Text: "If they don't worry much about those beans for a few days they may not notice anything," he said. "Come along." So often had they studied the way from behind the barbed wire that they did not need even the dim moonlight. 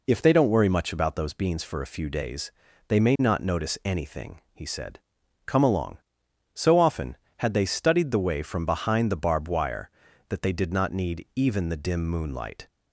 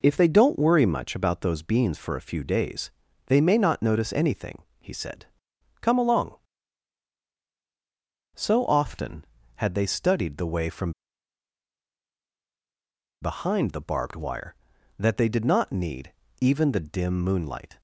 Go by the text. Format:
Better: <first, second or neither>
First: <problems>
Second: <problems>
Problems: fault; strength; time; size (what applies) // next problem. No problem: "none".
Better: first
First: pauses between "days" and "they"; at 2.4 s; 0.38 s long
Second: pauses between "days" and "they"; at 2.8 s; 0.38 s long // pauses between "from" and "behind"; strong; at 10.9 s; 2.3 s long // pauses between "need" and "even"; slight; at 16.1 s; 0.28 s long